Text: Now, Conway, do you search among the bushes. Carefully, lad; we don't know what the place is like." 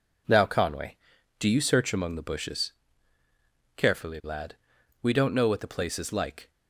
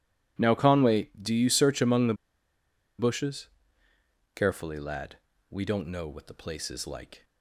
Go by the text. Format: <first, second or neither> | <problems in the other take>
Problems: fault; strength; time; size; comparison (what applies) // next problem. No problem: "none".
first | pauses between "the" and "bushes"; noticeable; at 2.1 s; 0.85 s long